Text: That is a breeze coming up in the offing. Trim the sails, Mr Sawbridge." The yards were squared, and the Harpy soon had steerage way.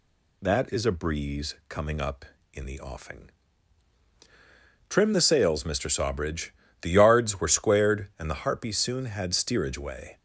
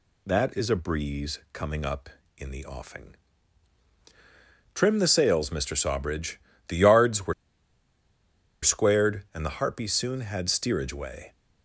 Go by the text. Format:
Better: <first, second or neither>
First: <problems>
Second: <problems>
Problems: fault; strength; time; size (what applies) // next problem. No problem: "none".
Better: first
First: none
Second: pauses between "were" and "squared"; strong; at 7.3 s; 1.2 s long